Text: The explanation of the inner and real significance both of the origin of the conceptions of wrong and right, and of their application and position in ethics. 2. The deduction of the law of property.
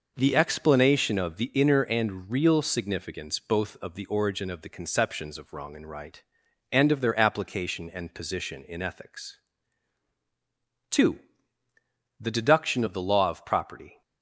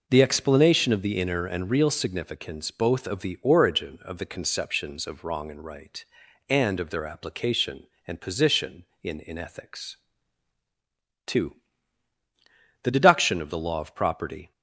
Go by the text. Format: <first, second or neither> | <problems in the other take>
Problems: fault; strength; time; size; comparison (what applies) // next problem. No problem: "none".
first | says "in" twice; at 9.1 s